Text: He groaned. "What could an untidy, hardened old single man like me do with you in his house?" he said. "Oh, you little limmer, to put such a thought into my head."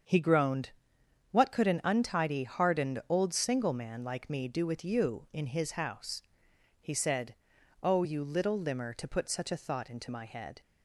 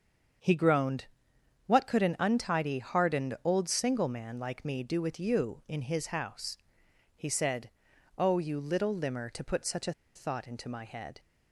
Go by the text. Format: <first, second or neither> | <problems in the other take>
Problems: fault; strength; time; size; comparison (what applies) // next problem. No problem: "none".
first | starts louder than the rest; strong; until 2.0 s; 7 dB; strong in the first // pauses between "a" and "thought"; slight; at 9.9 s; 0.23 s long